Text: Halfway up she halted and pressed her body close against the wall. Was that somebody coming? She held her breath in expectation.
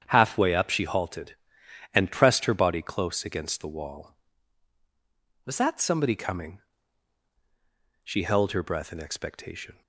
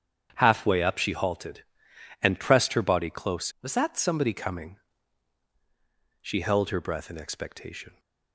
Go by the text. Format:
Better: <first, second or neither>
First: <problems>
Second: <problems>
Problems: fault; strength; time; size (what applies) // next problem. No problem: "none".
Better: first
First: starts louder than the rest; strong; until 1.0 s; 8.5 dB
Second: starts louder than the rest; strong; until 1.3 s; 8.5 dB // skips "against the wall"; at 3.5 s